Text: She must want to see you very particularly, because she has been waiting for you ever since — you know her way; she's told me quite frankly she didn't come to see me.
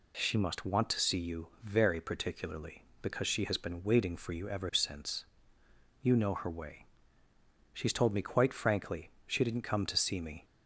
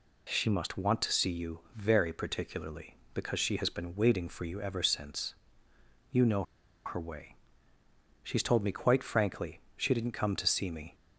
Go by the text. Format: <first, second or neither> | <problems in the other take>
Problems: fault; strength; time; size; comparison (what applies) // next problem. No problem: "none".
first | pauses between "know" and "her"; at 6.4 s; 0.41 s long // pauses between "frankly" and "she"; slight; at 9.6 s; 0.18 s long; slight in the first